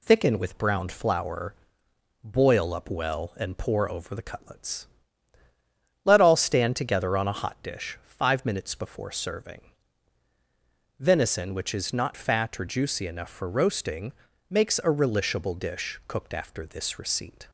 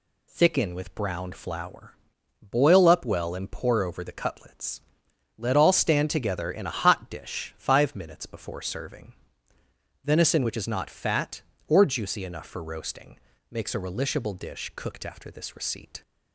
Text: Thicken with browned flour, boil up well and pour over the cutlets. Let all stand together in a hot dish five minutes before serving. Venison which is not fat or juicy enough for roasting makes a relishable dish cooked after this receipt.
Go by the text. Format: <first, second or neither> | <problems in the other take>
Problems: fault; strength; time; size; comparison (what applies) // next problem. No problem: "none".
second | says "on" for "in"; at 7.1 s // pauses between "roasting" and "makes"; at 14.1 s; 0.38 s long; slight in the second